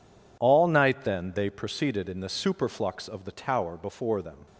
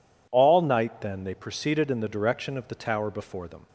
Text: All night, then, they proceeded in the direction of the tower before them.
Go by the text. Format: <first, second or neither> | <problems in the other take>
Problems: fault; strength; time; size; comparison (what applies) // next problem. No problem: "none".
second | says "superflux" for "direction"; at 2.2 s